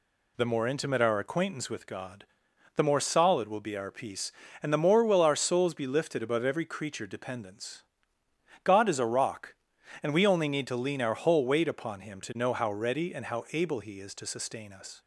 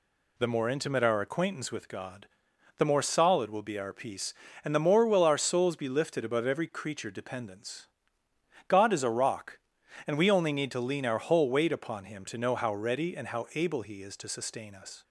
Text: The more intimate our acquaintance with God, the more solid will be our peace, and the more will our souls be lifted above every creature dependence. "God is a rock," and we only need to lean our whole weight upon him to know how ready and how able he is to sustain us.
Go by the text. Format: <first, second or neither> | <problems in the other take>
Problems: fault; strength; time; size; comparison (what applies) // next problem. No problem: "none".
neither | none